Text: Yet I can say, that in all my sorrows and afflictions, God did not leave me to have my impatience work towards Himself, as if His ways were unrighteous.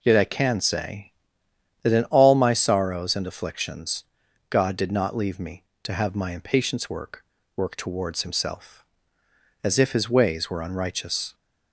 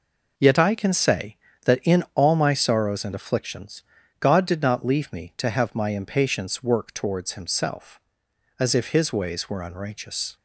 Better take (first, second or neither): second